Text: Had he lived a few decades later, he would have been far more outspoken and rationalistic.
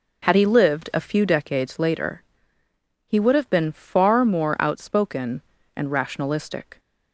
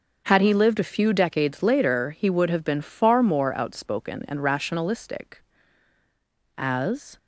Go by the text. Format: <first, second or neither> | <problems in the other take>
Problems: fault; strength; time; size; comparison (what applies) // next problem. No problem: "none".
first | starts louder than the rest; until 1.2 s; 6.5 dB // goes on to say "As"; from 6.5 s on; 0.60 s long